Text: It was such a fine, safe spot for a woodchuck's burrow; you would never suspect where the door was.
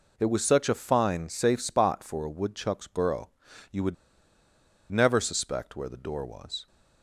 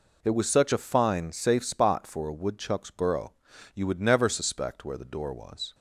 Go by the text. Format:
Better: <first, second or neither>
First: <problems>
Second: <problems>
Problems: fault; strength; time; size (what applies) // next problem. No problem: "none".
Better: second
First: pauses between "would" and "never"; noticeable; at 3.9 s; 0.97 s long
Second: none